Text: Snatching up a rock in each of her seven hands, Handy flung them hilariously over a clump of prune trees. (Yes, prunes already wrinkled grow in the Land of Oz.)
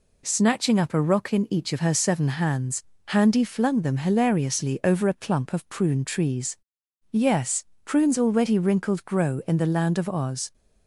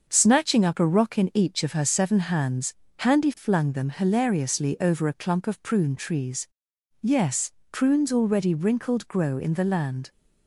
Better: first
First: none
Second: starts louder than the rest; until 1.1 s; 6.5 dB // stops before "of Oz"; at 10.0 s

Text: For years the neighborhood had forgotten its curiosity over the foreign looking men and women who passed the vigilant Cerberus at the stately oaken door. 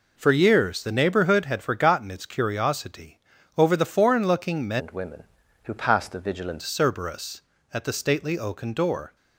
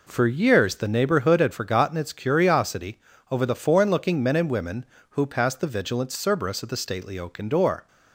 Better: second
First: pauses between "curiosity" and "over"; slight; at 3.1 s; 0.36 s long // changes voice from "and" to "vigilant"; from 4.7 to 6.6 s; 1.9 s long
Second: pauses between "curiosity" and "over"; slight; at 2.9 s; 0.32 s long

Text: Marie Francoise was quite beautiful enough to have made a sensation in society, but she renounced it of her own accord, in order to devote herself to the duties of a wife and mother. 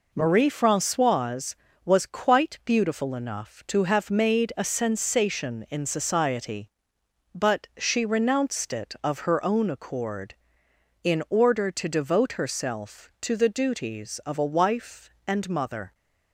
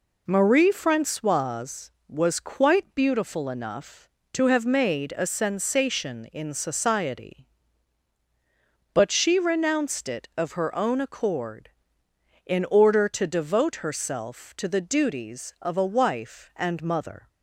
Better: neither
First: none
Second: none

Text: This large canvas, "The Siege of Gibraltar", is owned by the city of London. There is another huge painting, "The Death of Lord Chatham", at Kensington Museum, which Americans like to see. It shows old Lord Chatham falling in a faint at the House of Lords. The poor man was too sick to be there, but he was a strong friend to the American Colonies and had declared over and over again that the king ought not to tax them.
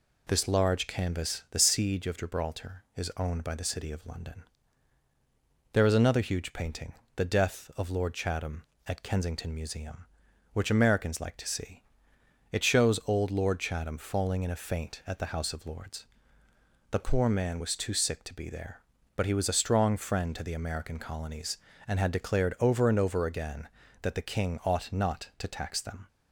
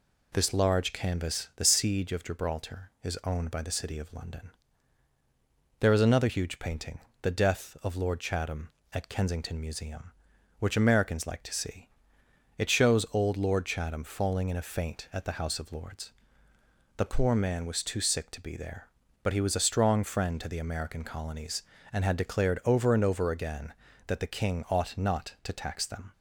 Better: neither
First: none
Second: none

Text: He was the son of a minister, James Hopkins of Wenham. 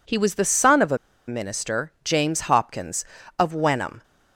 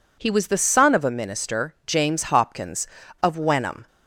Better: second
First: pauses between "a" and "minister"; slight; at 0.9 s; 0.31 s long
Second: none

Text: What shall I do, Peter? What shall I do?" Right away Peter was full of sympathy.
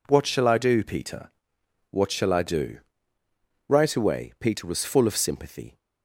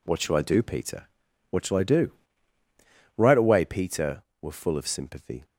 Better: first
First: none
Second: says "were" for "was"; at 4.4 s

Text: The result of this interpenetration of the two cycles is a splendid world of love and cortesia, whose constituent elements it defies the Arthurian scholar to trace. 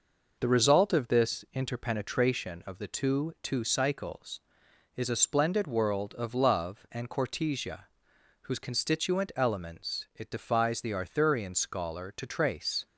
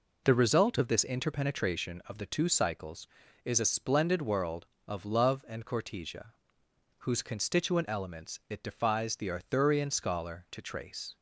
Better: second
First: says "two" twice; at 3.4 s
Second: none

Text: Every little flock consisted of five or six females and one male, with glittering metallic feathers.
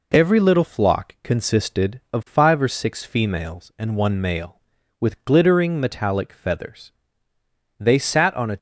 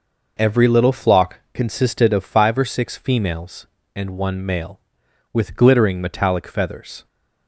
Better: second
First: goes on to say "They sat on a"; noticeable; from 7.7 s on; 0.80 s long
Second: none

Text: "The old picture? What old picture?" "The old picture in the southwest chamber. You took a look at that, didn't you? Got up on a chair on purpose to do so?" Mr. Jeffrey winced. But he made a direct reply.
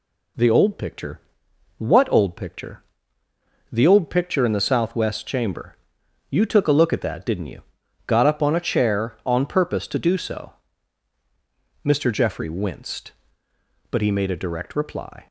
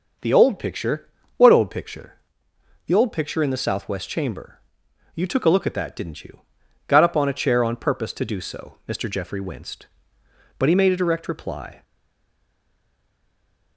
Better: first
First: none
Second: stays silent after the last word; noticeable; from 11.8 s on; 1.9 s long

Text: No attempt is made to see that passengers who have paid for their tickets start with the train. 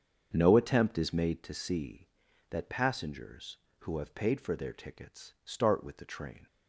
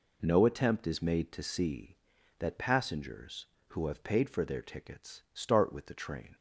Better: second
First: starts louder than the rest; strong; until 1.4 s; 7 dB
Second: none

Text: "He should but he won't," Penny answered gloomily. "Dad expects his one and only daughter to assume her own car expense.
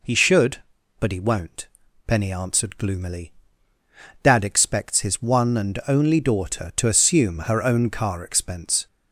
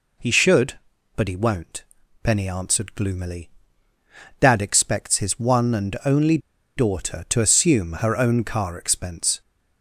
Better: first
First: none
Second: pauses between "only" and "daughter"; at 6.3 s; 0.37 s long

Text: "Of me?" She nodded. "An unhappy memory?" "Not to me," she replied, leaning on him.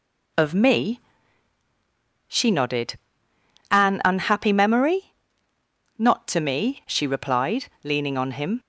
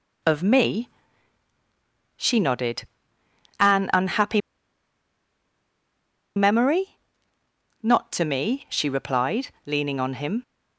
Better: first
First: none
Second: pauses between "unhappy" and "memory"; strong; at 4.4 s; 1.9 s long

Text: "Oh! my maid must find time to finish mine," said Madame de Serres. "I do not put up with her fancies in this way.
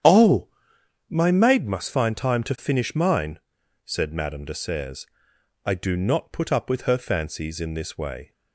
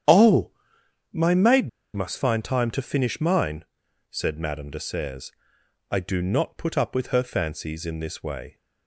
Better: first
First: starts louder than the rest; strong; until 1.6 s; 9.5 dB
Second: starts louder than the rest; strong; until 1.6 s; 9.5 dB // pauses between "maid" and "must"; slight; at 1.6 s; 0.25 s long

